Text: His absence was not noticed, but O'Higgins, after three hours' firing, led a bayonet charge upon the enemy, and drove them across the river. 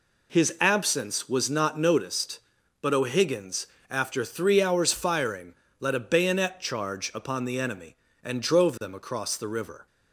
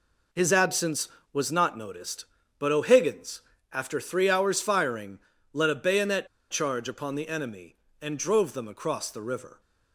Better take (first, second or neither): first